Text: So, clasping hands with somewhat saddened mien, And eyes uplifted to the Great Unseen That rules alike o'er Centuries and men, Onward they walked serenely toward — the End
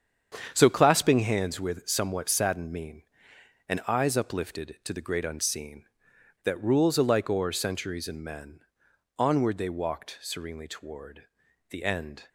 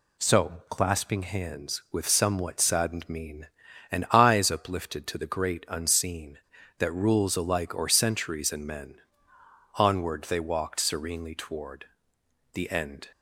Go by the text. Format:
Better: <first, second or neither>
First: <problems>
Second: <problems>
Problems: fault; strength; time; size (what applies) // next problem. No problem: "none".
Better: second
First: gets quieter; strong; throughout; 9.5 dB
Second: none